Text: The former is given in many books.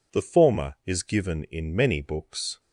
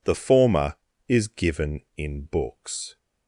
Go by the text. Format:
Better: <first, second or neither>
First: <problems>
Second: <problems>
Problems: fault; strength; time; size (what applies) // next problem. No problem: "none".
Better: first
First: none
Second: skips "many"; at 2.2 s